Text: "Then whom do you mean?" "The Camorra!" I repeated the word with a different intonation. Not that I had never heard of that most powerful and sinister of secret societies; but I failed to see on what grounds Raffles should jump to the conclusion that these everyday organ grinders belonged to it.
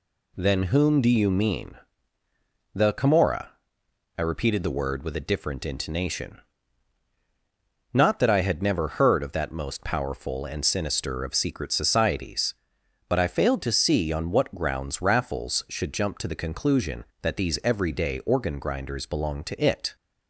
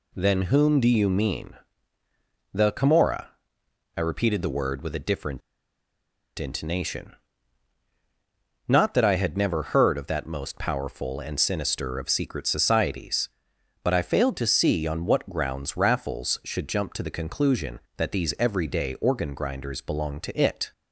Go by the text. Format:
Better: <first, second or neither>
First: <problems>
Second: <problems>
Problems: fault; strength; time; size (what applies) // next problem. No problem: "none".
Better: first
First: none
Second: pauses between "different" and "intonation"; noticeable; at 5.4 s; 0.97 s long